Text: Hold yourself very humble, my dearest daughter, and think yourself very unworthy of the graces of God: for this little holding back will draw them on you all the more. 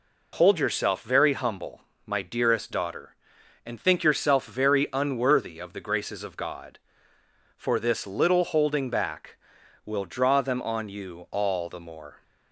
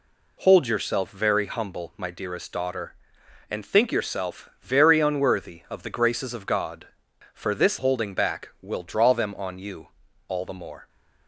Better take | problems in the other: first | skips "little"; at 7.7 s // pauses between "you" and "all"; at 9.8 s; 0.40 s long

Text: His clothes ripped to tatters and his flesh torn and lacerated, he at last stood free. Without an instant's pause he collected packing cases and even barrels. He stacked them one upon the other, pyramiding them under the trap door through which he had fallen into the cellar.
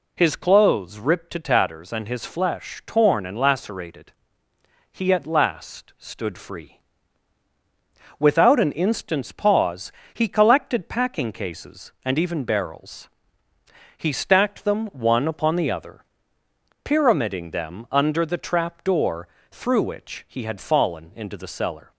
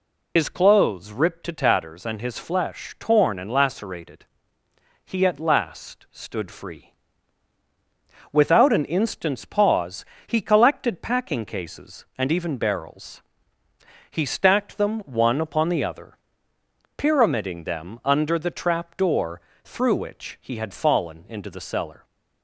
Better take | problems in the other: first | loses the start of "His"; at 0.3 s; 75 ms // pauses between "pause" and "he"; slight; at 10.0 s; 0.22 s long; slight in the first // pauses between "door" and "through"; slight; at 19.3 s; 0.24 s long; slight in the first

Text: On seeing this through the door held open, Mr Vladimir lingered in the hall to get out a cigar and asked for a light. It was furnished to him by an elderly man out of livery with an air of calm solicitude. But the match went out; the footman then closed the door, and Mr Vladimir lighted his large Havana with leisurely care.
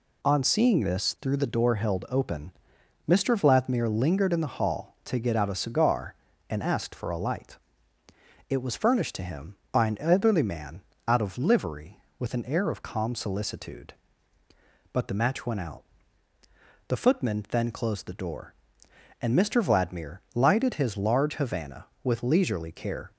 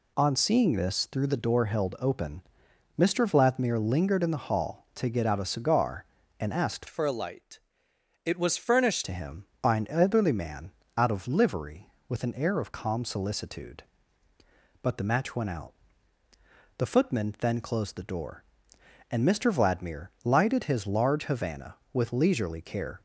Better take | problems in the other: first | changes voice from "for" to "furnished"; from 6.8 to 9.0 s; 2.2 s long // pauses between "man" and "out"; slight; at 10.7 s; 0.28 s long; slight in the first

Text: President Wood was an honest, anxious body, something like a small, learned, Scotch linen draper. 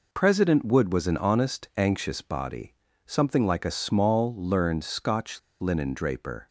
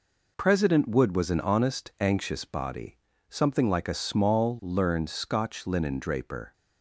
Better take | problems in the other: second | pauses between "Scotch" and "linen"; slight; at 5.3 s; 0.21 s long

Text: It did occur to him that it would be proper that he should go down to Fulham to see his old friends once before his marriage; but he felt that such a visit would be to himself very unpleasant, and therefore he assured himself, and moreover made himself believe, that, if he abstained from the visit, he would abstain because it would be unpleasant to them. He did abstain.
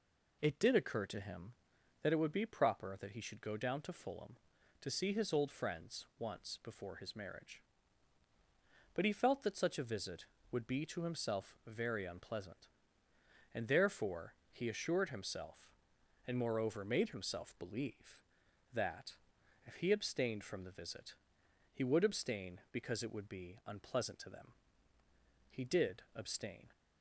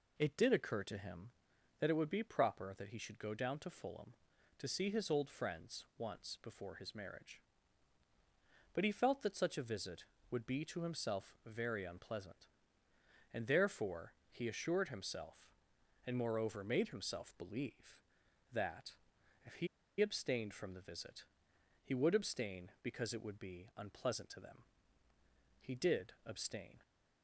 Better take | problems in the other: first | pauses between "therefore" and "he"; slight; at 14.1 s; 0.18 s long; slight in the first // pauses between "he" and "abstained"; slight; at 19.6 s; 0.33 s long

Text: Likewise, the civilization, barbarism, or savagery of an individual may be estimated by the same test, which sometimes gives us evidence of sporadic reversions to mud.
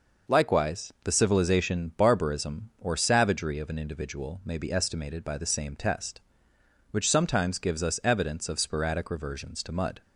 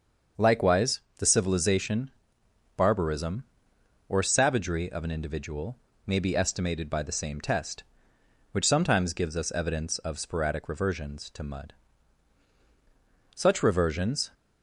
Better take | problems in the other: first | starts louder than the rest; until 1.5 s; 6.5 dB // pauses between "individual" and "may"; slight; at 5.7 s; 0.30 s long // goes on to say "Such reversions"; noticeable; from 13.3 s on; 0.98 s long

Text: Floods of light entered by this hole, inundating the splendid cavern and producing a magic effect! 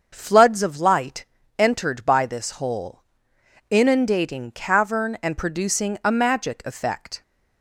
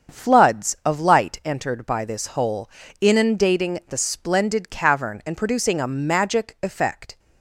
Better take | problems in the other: second | starts louder than the rest; until 1.1 s; 6.5 dB; strong in the second // pauses between "light" and "entered"; slight; at 1.2 s; 0.32 s long // skips "the splendid"; at 4.5 s

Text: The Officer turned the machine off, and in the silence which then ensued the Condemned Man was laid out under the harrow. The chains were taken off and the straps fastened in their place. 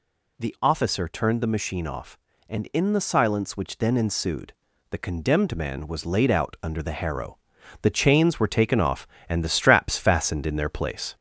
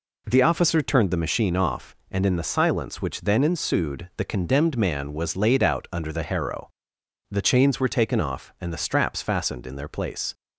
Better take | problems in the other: second | gets louder; slight; throughout; 2.5 dB // pauses between "ensued" and "the"; slight; at 4.5 s; 0.36 s long

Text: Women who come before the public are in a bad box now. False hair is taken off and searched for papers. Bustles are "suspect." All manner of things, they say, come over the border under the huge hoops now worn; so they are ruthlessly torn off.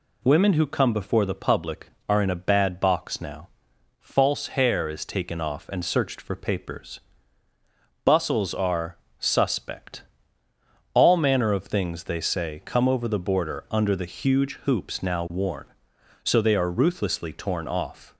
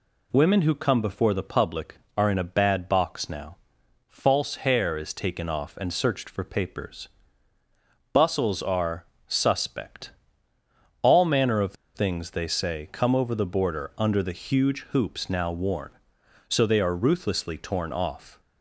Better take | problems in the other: first | pauses between "are" and "suspect"; slight; at 9.0 s; 0.24 s long; slight in the first // pauses between "of" and "things"; slight; at 11.7 s; 0.21 s long

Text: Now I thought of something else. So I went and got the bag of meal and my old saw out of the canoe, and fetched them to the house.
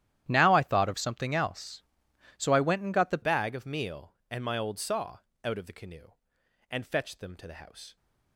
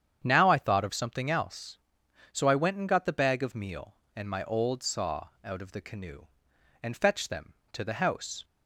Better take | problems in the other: second | starts louder than the rest; strong; until 1.2 s; 11.5 dB; strong in the second // changes voice at "bag"; from 3.2 s on; 4.7 s long // pauses between "saw" and "out"; slight; at 5.1 s; 0.26 s long

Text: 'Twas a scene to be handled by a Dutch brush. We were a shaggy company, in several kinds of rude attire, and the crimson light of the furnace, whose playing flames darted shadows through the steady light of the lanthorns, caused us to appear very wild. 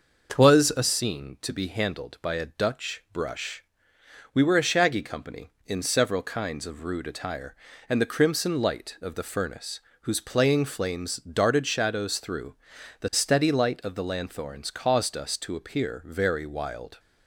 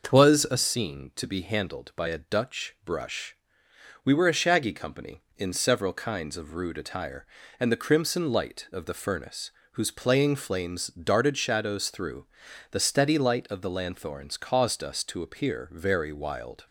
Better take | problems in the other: neither | pauses between "through" and "the"; noticeable; the same in both

